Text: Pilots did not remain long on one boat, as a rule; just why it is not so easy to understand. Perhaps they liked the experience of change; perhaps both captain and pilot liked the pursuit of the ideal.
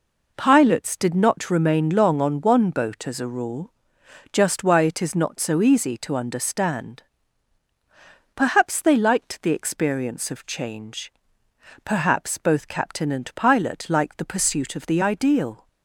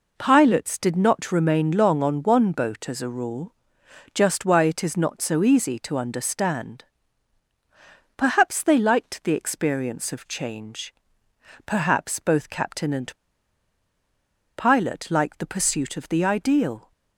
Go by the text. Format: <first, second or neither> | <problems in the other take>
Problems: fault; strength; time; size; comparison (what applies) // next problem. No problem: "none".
first | pauses between "and" and "pilot"; strong; at 13.1 s; 1.4 s long